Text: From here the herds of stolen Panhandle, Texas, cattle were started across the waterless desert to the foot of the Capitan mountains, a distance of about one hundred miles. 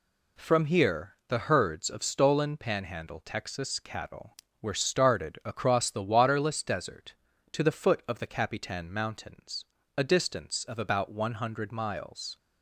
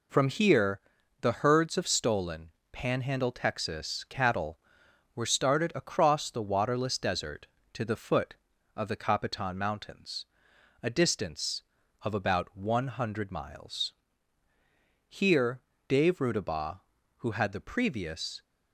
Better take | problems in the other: first | pauses between "here" and "the"; at 0.8 s; 0.40 s long // pauses between "stolen" and "Panhandle"; slight; at 2.5 s; 0.22 s long // goes on to say "Here Dave Rudabaugh who had the previous"; strong; from 15.0 s on; 3.3 s long

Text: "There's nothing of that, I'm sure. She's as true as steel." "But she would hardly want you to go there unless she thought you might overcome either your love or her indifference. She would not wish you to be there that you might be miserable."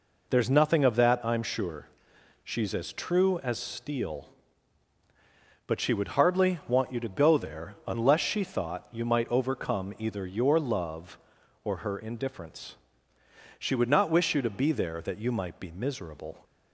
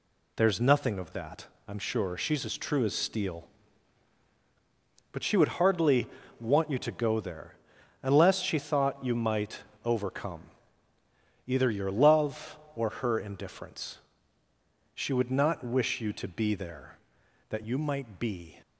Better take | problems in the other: first | pauses between "hardly" and "want"; slight; at 6.0 s; 0.32 s long // pauses between "there" and "unless"; noticeable; at 7.5 s; 0.48 s long // pauses between "might" and "overcome"; slight; at 9.6 s; 0.22 s long // pauses between "overcome" and "either"; at 10.4 s; 1.0 s long // stops before "miserable"; at 18.6 s

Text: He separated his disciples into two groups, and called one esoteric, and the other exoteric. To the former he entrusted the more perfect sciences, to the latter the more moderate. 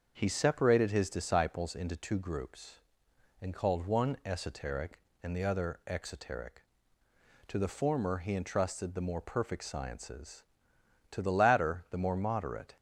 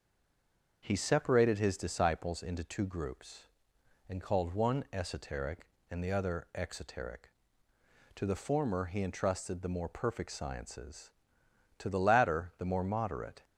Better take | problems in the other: first | stays silent before the first word; slight; until 0.8 s; 0.8 s long // starts louder than the rest; until 1.8 s; 6.5 dB; also in the first

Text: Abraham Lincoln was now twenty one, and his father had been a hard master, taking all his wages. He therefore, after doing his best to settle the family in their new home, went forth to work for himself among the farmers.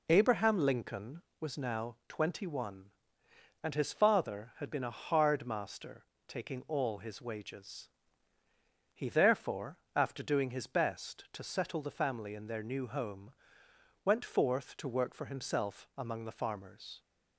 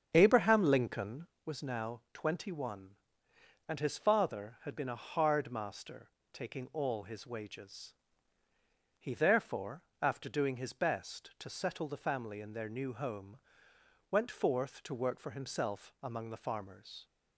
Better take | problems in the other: first | starts louder than the rest; strong; until 1.4 s; 7.5 dB

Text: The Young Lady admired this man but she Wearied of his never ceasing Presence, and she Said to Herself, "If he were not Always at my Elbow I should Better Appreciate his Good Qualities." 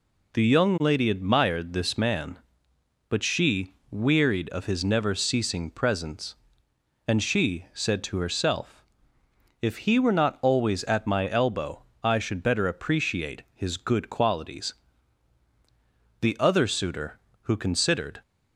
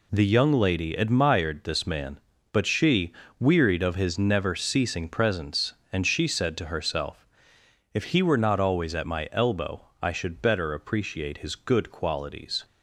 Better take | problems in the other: second | pauses between "she" and "Wearied"; slight; at 3.7 s; 0.16 s long; slight in the second // pauses between "Elbow" and "I"; slight; at 11.8 s; 0.20 s long; slight in the second // goes on to say "The Other Suitor who considered"; strong; from 16.2 s on; 2.0 s long

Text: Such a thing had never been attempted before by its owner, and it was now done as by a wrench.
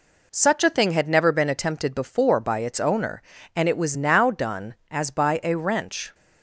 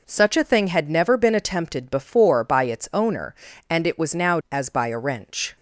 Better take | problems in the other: first | skips "done"; at 4.4 s

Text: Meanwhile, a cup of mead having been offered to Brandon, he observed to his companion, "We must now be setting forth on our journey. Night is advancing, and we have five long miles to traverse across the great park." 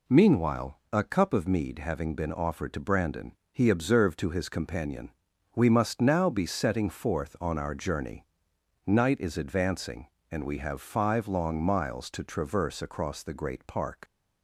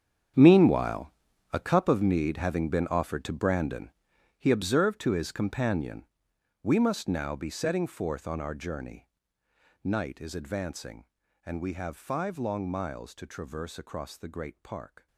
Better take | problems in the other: first | gets quieter; strong; throughout; 15 dB

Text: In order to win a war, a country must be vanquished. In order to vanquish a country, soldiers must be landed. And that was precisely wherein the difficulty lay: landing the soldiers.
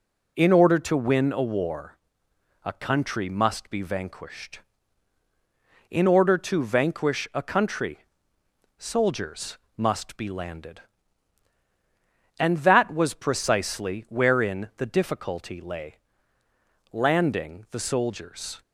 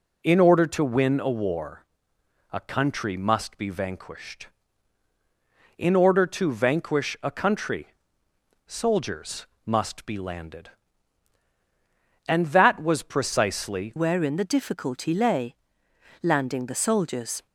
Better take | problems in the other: first | pauses between "soldiers" and "must"; slight; at 9.4 s; 0.18 s long; slight in the first // changes voice at "wherein"; from 13.9 s on; 3.5 s long

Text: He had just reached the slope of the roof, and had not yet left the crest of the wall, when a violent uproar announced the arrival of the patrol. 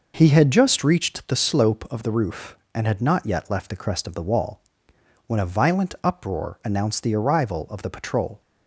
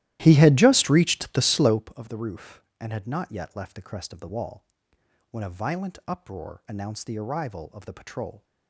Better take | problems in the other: first | starts louder than the rest; strong; until 1.8 s; 15 dB

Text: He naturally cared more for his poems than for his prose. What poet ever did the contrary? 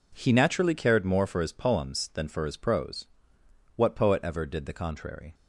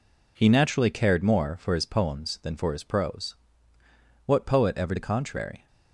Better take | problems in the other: first | skips "did"; at 4.9 s

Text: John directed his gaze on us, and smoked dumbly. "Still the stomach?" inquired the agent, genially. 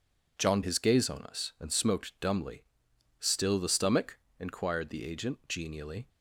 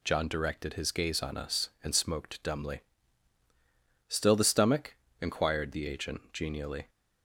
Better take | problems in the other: second | skips "directed"; at 0.6 s

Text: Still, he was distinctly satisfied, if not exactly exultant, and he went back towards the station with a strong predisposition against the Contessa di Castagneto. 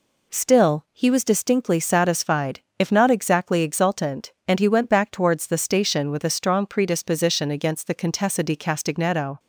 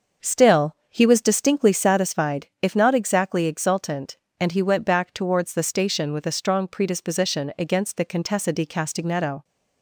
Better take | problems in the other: first | starts louder than the rest; until 2.0 s; 6.5 dB

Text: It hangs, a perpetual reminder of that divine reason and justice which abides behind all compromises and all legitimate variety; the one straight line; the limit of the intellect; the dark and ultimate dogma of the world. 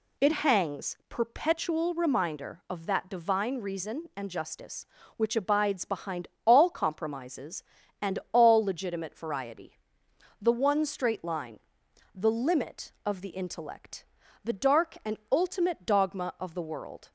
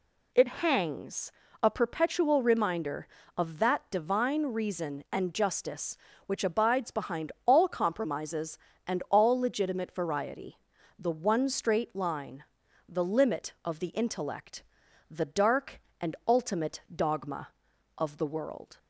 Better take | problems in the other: second | skips "a"; at 1.0 s // pauses between "behind" and "all"; slight; at 6.2 s; 0.18 s long

